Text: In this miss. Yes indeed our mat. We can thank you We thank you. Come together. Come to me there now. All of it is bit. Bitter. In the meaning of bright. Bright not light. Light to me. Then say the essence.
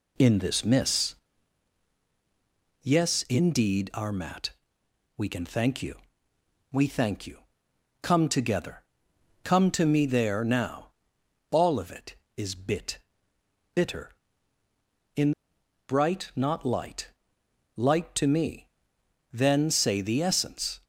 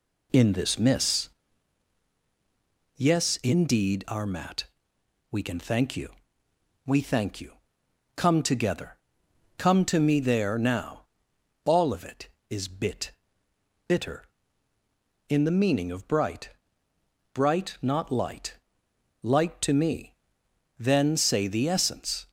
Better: second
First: pauses between "you" and "We"; noticeable; at 5.9 s; 0.76 s long // skips "the meaning of bright"; at 15.5 s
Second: pauses between "you" and "We"; noticeable; at 6.1 s; 0.76 s long

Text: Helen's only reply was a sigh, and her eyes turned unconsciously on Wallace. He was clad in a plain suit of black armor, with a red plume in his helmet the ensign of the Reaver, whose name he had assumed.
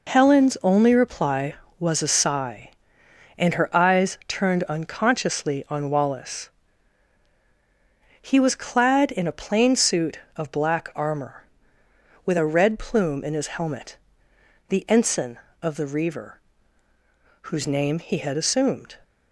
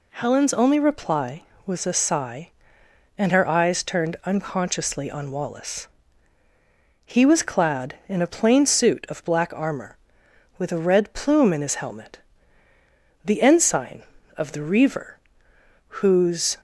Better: first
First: pauses between "helmet" and "the"; noticeable; at 13.9 s; 0.72 s long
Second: pauses between "helmet" and "the"; at 12.1 s; 1.0 s long // stops before "name he had assumed"; at 16.5 s

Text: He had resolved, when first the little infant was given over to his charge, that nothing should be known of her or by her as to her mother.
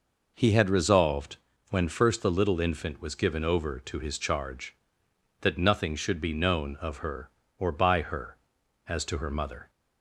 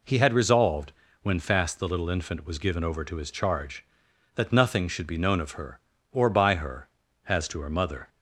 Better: first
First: none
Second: says "fast" for "first"; at 1.3 s

